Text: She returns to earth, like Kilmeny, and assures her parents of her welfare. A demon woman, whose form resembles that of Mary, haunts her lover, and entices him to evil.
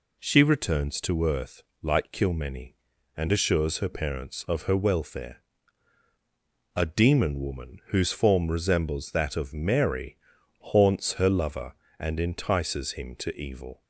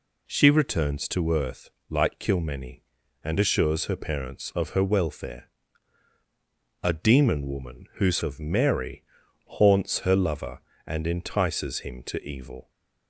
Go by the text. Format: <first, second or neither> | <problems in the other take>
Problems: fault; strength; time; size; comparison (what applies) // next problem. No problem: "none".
first | skips "form resembles that"; at 8.2 s